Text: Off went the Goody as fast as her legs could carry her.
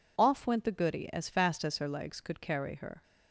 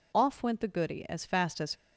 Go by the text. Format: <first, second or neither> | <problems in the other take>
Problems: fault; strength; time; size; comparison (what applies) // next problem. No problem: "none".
first | stops before "her legs could carry her"; at 1.7 s